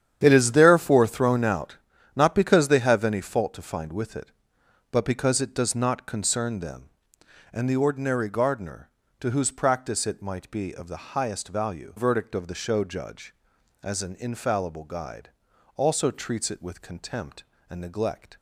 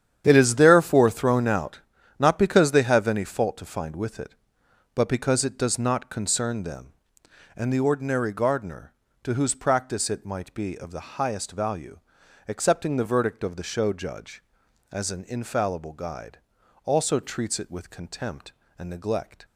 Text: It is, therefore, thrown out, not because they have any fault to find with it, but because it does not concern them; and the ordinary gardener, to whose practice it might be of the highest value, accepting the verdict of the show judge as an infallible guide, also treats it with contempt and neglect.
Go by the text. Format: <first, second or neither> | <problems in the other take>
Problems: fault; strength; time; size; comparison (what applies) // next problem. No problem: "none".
second | starts louder than the rest; strong; until 1.2 s; 9.5 dB; strong in the second // skips "accepting the"; at 11.9 s